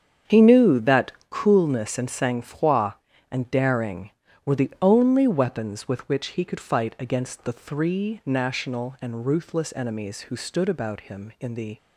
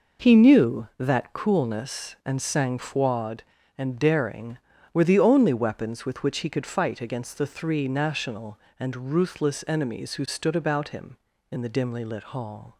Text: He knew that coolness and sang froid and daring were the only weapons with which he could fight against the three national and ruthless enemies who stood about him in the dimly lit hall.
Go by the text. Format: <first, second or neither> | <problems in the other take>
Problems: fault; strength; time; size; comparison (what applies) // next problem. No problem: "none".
second | starts louder than the rest; strong; until 1.4 s; 8 dB // pauses between "that" and "coolness"; slight; at 1.1 s; 0.18 s long // stops before "dimly lit hall"; at 11.7 s